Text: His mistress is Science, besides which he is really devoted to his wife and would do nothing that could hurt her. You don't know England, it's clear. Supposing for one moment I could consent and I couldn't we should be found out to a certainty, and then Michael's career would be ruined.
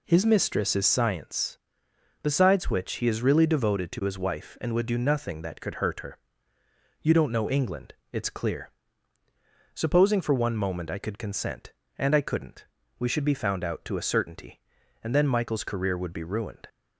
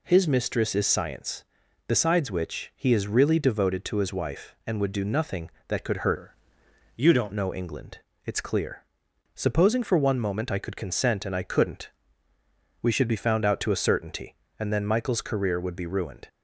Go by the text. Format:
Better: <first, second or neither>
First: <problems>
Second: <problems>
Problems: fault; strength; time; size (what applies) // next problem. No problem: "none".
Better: first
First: pauses between "couldn't" and "we"; slight; at 12.6 s; 0.34 s long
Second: changes voice from "her" to "don't"; from 6.1 to 7.3 s; 1.2 s long // pauses between "couldn't" and "we"; noticeable; at 11.8 s; 0.92 s long